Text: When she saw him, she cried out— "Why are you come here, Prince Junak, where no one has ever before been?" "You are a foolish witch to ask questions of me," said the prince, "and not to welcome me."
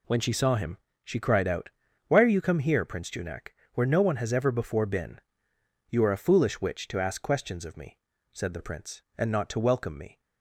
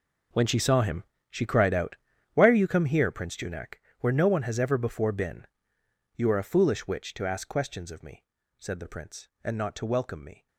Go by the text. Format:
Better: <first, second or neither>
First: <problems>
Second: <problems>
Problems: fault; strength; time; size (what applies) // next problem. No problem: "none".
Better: first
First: none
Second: gets quieter; strong; throughout; 15.5 dB